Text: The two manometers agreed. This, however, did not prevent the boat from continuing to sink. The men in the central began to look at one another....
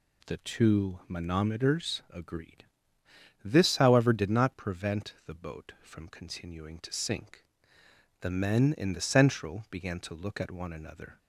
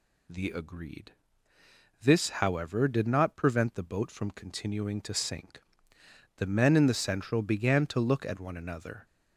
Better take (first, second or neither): first